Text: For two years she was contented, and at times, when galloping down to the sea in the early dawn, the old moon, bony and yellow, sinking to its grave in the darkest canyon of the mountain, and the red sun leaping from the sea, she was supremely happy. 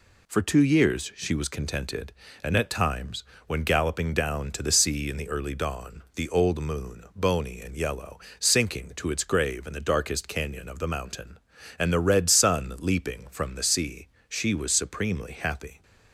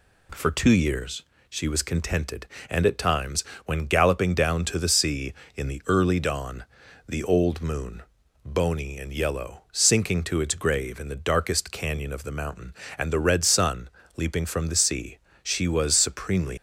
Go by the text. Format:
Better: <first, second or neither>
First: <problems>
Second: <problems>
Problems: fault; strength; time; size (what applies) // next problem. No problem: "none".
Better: first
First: none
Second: pauses between "years" and "she"; slight; at 1.2 s; 0.26 s long // pauses between "sun" and "leaping"; slight; at 13.8 s; 0.28 s long // stops before "happy"; at 16.5 s